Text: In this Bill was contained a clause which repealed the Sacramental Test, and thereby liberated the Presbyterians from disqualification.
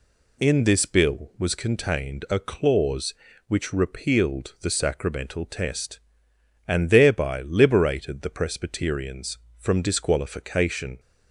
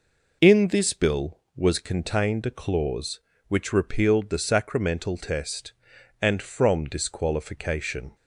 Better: first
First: none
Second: skips "thereby liberated the Presbyterians"; at 6.4 s

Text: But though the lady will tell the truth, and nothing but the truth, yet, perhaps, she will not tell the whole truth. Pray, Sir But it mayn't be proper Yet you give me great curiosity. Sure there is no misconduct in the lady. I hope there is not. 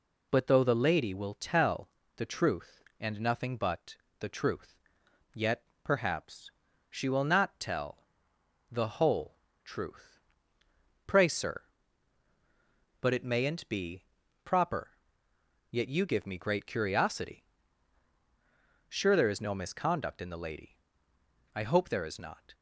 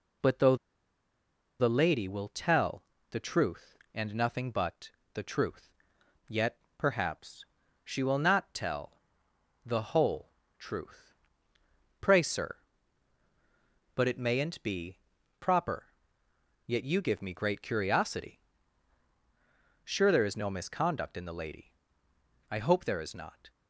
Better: first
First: pauses between "tell" and "the"; slight; at 1.8 s; 0.28 s long // pauses between "but" and "the"; slight; at 3.9 s; 0.24 s long // pauses between "tell" and "the"; noticeable; at 7.9 s; 0.70 s long // pauses between "whole" and "truth"; slight; at 9.3 s; 0.28 s long // pauses between "be" and "proper"; at 14.0 s; 0.41 s long // pauses between "proper" and "Yet"; noticeable; at 14.8 s; 0.82 s long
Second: pauses between "though" and "the"; at 0.5 s; 1.0 s long // pauses between "tell" and "the"; slight; at 2.8 s; 0.28 s long // pauses between "but" and "the"; slight; at 4.9 s; 0.24 s long // pauses between "tell" and "the"; noticeable; at 8.9 s; 0.70 s long // pauses between "whole" and "truth"; slight; at 10.3 s; 0.28 s long // pauses between "be" and "proper"; at 14.9 s; 0.40 s long // pauses between "proper" and "Yet"; noticeable; at 15.8 s; 0.82 s long

